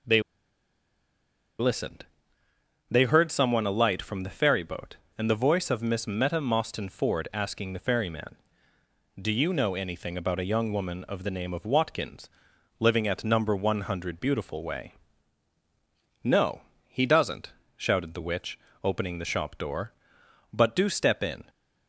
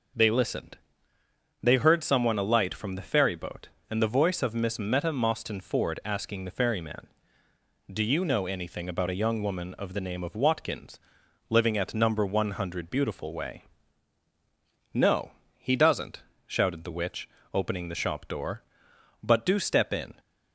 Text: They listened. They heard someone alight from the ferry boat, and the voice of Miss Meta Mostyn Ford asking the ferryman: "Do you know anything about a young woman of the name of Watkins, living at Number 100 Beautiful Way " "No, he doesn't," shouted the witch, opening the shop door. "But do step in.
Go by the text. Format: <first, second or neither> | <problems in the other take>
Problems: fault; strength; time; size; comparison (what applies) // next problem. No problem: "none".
second | starts louder than the rest; noticeable; until 3.3 s; 6 dB // pauses between "They" and "listened"; strong; at 0.2 s; 1.3 s long